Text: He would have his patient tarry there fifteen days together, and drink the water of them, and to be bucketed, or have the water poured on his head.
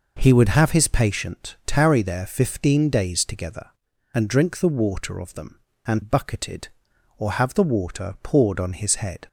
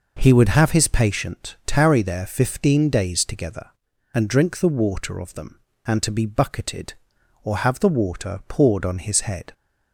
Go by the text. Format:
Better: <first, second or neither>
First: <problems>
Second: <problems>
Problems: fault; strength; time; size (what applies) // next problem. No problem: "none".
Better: second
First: skips "to be"; at 6.0 s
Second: none